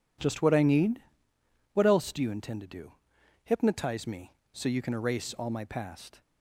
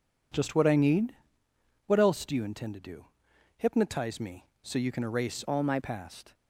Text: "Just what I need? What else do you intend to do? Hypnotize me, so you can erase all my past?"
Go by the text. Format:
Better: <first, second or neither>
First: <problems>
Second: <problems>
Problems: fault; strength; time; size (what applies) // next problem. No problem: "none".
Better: first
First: none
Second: changes voice from "all" to "my"; from 5.4 to 5.7 s; 0.3 s long